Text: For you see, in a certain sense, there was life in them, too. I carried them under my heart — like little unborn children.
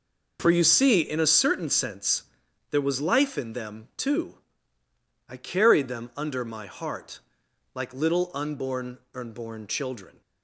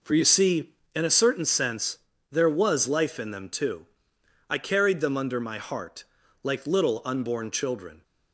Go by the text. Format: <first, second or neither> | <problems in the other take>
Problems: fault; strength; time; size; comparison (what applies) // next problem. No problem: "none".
second | says "unborn" twice; at 9.1 s